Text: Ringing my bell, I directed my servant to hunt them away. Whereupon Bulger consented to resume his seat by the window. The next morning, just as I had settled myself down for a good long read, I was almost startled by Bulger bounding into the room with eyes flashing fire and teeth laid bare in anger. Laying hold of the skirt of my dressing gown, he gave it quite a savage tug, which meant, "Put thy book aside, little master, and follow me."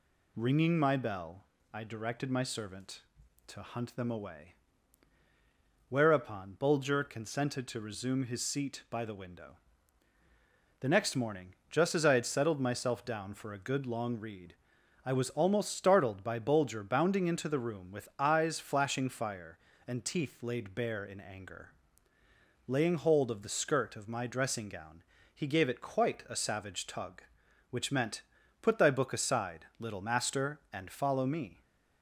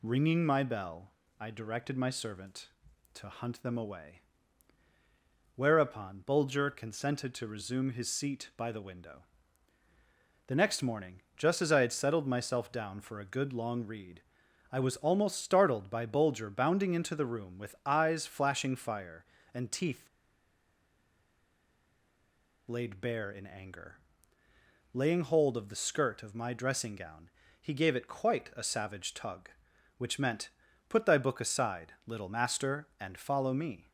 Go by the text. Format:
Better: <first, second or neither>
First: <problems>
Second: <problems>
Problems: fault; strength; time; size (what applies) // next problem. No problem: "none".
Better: first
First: none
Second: pauses between "teeth" and "laid"; strong; at 20.0 s; 2.6 s long